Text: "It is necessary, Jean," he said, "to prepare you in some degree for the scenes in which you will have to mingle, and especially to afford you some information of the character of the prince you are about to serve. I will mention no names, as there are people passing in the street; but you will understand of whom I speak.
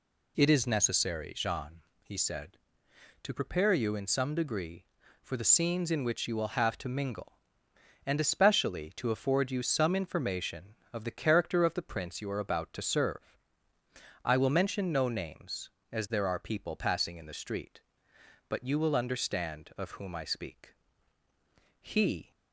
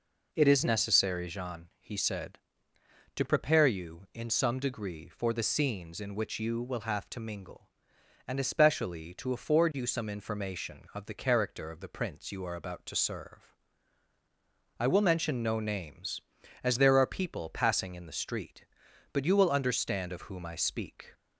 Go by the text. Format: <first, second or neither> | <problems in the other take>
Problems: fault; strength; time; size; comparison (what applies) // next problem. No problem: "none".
second | goes on to say "He"; from 21.8 s on; 0.50 s long